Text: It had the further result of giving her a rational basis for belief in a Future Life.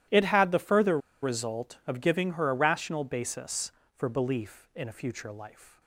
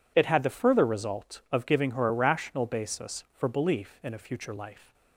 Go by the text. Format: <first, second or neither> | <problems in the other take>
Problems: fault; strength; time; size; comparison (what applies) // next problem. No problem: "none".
second | starts louder than the rest; strong; until 1.3 s; 12.5 dB // pauses between "further" and "result"; slight; at 0.9 s; 0.24 s long